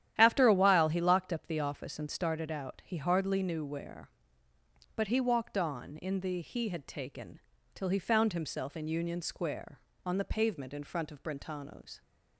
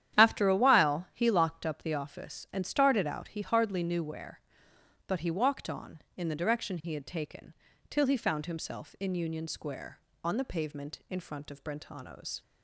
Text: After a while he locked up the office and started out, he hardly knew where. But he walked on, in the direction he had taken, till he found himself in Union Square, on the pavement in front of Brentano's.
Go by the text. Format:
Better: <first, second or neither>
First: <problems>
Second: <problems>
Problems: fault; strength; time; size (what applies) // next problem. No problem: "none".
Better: second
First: starts louder than the rest; strong; until 1.1 s; 11 dB // skips "direction"; at 6.4 s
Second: starts louder than the rest; strong; until 1.2 s; 10.5 dB